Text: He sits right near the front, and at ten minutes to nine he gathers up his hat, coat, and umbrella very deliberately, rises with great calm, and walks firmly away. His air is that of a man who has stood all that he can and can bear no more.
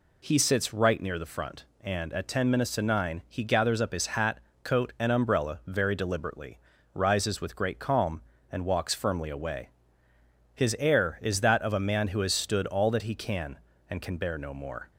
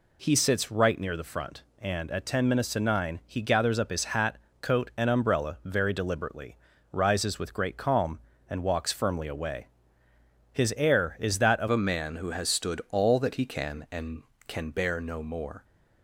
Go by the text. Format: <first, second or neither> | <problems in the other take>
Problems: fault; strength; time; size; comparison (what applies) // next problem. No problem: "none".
first | changes voice at "a"; from 11.6 s on; 4.0 s long